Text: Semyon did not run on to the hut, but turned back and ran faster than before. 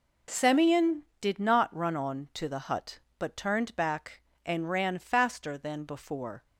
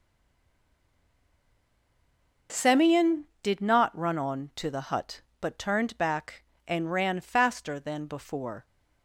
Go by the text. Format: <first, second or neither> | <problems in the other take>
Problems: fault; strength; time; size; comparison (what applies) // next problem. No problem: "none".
first | stays silent before the first word; until 2.4 s; 2.4 s long